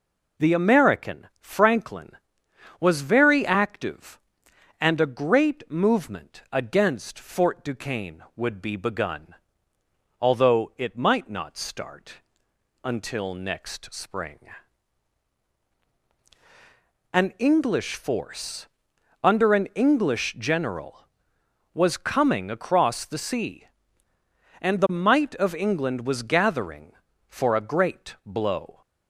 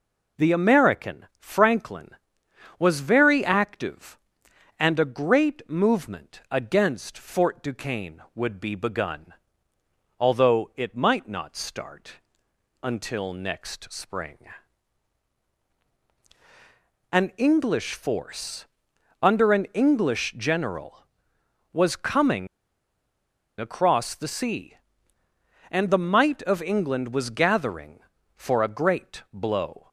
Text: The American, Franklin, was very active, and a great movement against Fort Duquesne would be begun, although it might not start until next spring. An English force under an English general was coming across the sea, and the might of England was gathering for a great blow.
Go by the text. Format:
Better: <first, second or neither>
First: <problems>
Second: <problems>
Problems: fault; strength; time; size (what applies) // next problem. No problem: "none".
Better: first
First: pauses between "start" and "until"; noticeable; at 12.1 s; 0.68 s long // pauses between "force" and "under"; noticeable; at 18.6 s; 0.56 s long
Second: pauses between "start" and "until"; noticeable; at 12.1 s; 0.68 s long // pauses between "force" and "under"; noticeable; at 18.6 s; 0.56 s long // pauses between "coming" and "across"; at 22.4 s; 1.1 s long